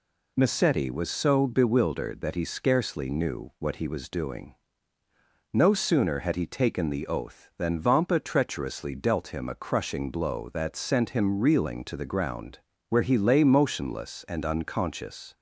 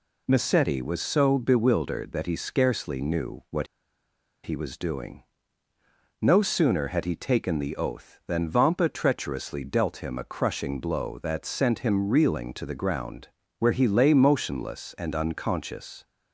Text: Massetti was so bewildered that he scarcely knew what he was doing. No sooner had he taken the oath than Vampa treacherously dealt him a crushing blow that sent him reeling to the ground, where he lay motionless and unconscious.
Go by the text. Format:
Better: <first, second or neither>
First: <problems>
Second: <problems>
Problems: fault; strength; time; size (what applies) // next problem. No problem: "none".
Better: first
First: none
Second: pauses between "what" and "he"; noticeable; at 3.6 s; 0.77 s long